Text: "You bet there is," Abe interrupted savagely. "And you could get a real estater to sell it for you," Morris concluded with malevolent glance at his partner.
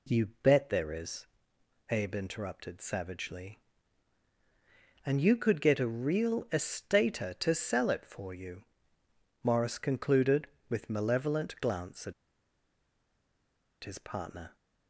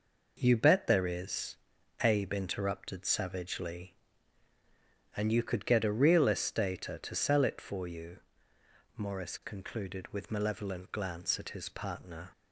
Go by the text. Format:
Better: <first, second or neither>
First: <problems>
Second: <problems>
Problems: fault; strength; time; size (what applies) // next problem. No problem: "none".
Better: second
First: pauses between "at" and "his"; strong; at 12.1 s; 1.6 s long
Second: none